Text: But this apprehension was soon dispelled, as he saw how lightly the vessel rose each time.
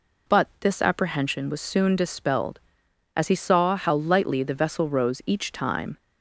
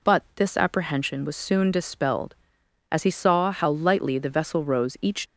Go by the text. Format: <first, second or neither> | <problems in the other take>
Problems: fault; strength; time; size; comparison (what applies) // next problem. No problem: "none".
first | stops before "time"; at 5.2 s